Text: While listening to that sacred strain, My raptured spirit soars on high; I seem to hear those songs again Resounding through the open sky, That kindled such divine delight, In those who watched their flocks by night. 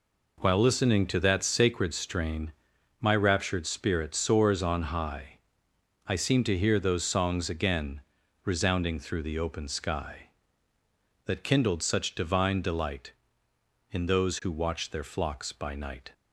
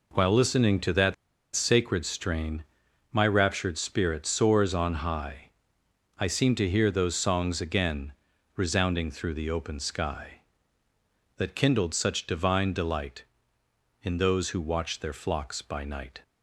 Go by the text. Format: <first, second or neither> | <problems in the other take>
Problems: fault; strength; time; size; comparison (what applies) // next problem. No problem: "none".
first | pauses between "that" and "sacred"; at 1.1 s; 0.39 s long // pauses between "again" and "Resounding"; at 8.1 s; 0.42 s long; also in the first